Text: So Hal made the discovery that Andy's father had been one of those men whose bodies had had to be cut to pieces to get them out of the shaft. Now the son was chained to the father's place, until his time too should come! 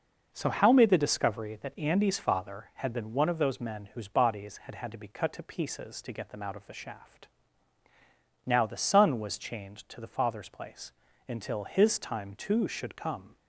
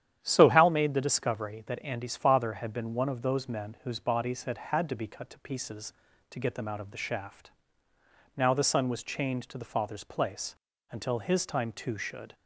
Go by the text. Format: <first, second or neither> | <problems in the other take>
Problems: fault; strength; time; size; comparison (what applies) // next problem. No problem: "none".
first | starts louder than the rest; strong; until 1.2 s; 10 dB // stops before "come"; at 12.3 s